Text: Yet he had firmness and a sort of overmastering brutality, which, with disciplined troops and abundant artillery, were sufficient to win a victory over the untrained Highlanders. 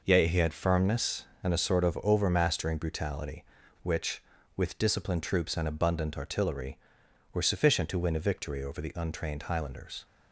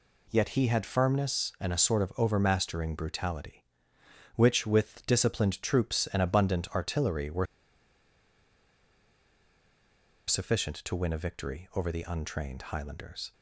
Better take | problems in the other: first | pauses between "were" and "sufficient"; strong; at 7.4 s; 2.8 s long

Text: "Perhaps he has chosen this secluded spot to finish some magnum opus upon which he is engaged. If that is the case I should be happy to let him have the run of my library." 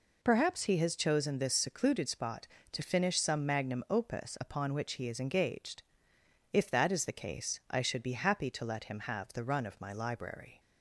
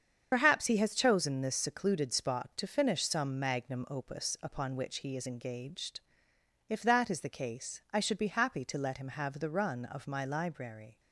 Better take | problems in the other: first | loses the start of "Perhaps"; at 0.3 s; 70 ms // starts louder than the rest; strong; until 1.3 s; 7.5 dB

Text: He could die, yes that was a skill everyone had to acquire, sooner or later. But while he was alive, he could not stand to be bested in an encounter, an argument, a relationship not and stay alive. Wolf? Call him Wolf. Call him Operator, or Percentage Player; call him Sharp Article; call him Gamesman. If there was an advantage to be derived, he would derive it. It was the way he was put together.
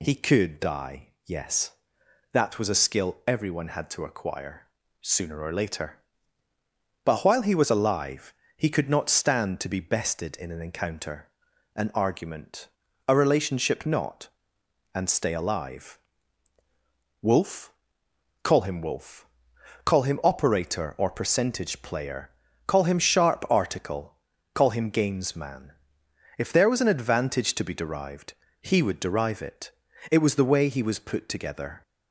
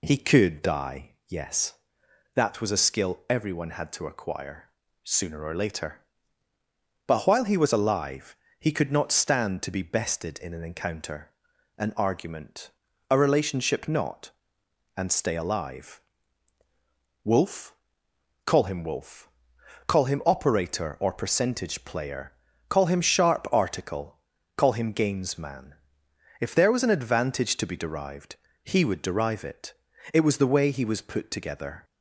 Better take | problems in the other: first | starts louder than the rest; slight; until 1.3 s; 2 dB

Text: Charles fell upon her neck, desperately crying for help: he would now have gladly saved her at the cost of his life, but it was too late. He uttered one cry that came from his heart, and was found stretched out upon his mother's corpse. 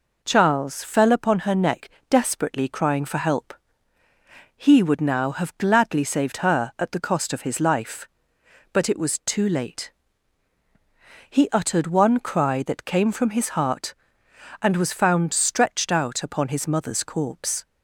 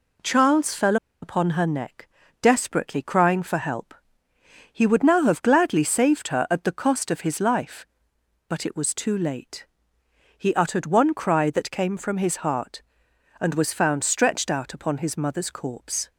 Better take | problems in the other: first | pauses between "fell" and "upon"; slight; at 0.9 s; 0.26 s long

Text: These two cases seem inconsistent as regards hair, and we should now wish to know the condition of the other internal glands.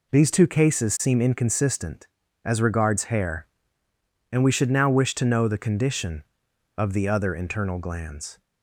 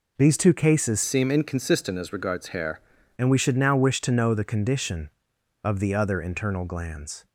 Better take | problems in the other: first | changes voice from "seem" to "hair"; from 1.0 to 2.7 s; 1.7 s long

